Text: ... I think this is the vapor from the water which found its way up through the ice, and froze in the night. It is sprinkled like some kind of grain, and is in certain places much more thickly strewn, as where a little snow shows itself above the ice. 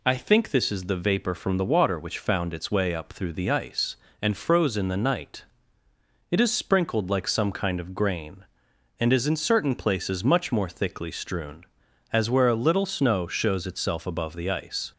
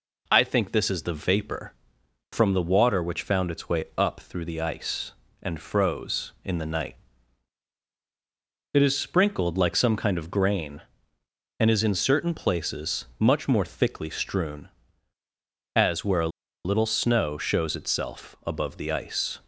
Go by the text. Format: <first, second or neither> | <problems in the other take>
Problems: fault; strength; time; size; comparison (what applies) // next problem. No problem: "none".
first | pauses between "places" and "much"; slight; at 13.0 s; 0.16 s long // pauses between "a" and "little"; at 16.2 s; 0.36 s long